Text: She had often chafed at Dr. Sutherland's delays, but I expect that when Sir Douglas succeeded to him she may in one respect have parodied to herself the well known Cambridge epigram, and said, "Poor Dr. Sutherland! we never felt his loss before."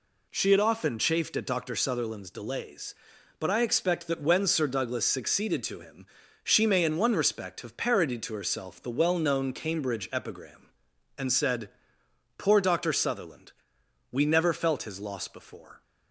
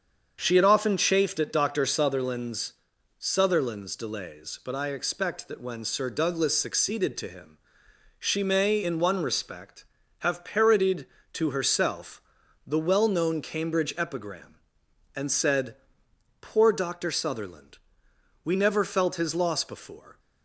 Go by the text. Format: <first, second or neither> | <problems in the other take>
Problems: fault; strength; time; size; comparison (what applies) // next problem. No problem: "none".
first | starts louder than the rest; strong; until 1.4 s; 7 dB // says "Sutherland's" twice; at 3.1 s // pauses between "him" and "she"; noticeable; at 7.5 s; 0.60 s long; also in the first // pauses between "herself" and "the"; at 12.2 s; 0.42 s long